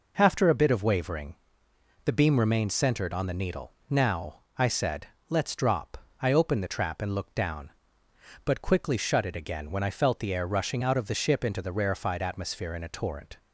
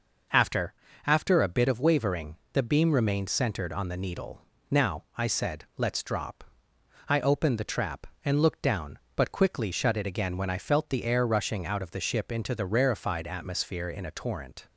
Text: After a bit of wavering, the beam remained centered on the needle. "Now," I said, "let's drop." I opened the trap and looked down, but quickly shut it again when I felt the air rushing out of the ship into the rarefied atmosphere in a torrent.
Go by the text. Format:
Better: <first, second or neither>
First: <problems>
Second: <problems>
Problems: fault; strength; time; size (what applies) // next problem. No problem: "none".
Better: first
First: none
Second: says "After" twice; at 1.0 s